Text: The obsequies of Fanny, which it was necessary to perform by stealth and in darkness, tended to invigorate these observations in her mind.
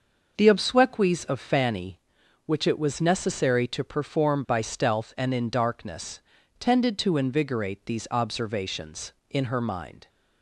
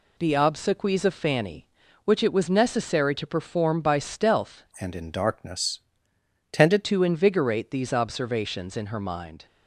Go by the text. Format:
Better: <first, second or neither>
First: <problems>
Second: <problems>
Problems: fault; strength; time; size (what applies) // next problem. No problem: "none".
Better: first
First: none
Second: changes voice from "and" to "tended"; from 4.8 to 6.8 s; 2.0 s long